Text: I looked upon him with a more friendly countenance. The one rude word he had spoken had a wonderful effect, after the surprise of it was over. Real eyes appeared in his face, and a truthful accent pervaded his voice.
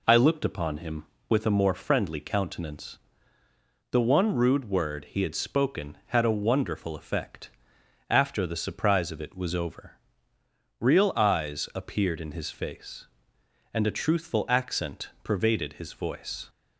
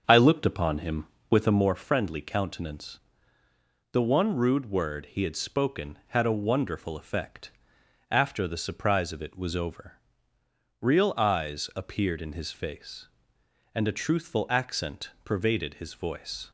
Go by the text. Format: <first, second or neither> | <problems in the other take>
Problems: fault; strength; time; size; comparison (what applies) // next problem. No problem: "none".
first | starts louder than the rest; until 1.7 s; 7 dB